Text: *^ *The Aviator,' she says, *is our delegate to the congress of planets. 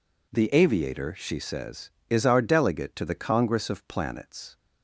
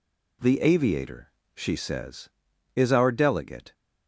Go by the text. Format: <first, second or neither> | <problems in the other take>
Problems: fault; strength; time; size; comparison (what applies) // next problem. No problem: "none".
first | stops before "to the congress of planets"; at 3.7 s